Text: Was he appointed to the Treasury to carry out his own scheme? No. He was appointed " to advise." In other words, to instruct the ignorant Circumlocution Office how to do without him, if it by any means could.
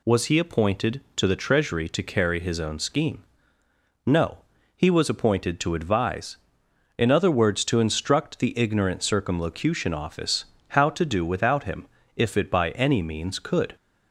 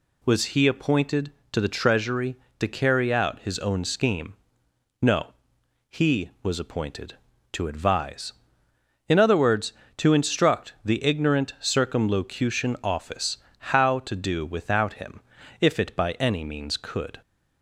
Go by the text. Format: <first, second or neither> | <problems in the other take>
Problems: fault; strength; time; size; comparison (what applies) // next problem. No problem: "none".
second | skips "out"; at 2.4 s // pauses between "Office" and "how"; slight; at 10.4 s; 0.28 s long; slight in the second